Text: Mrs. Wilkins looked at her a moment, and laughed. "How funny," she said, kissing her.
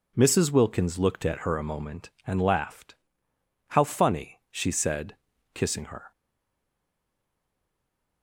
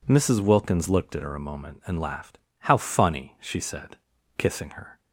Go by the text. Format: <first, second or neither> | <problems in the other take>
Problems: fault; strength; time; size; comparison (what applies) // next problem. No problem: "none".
second | stays silent after the last word; from 6.1 s on; 2.1 s long